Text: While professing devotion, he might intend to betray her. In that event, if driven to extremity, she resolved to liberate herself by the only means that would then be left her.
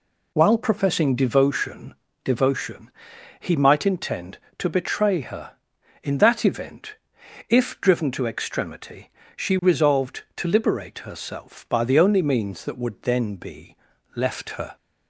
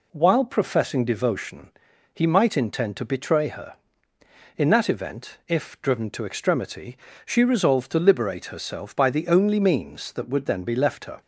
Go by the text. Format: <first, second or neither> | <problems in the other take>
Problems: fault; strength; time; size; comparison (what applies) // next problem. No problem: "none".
second | says "devotion" twice; at 2.2 s // pauses between "be" and "left"; slight; at 13.7 s; 0.36 s long